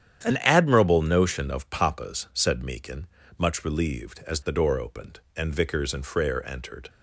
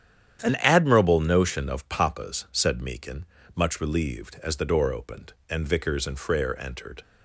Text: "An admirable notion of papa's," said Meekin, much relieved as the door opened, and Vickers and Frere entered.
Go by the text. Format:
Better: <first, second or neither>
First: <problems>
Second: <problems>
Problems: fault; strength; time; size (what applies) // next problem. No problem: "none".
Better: neither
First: starts louder than the rest; strong; until 1.2 s; 9.5 dB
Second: starts louder than the rest; strong; until 1.4 s; 9.5 dB